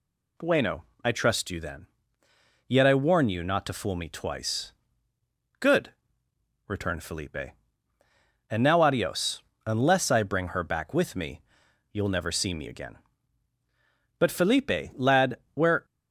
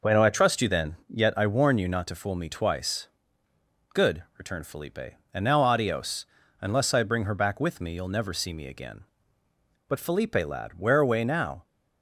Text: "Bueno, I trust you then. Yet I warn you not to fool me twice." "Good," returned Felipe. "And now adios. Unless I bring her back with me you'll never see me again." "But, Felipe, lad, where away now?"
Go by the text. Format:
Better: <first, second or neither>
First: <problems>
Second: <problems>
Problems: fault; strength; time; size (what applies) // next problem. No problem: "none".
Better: second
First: pauses between "me" and "you'll"; noticeable; at 11.4 s; 0.52 s long // stops before "away now"; at 15.8 s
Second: none